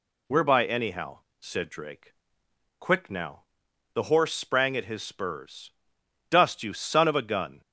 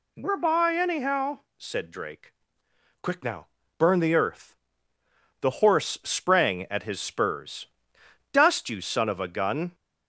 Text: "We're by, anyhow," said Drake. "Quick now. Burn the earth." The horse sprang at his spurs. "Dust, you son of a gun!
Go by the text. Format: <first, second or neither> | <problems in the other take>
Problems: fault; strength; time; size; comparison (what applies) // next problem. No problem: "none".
second | skips "Burn the earth"; at 3.6 s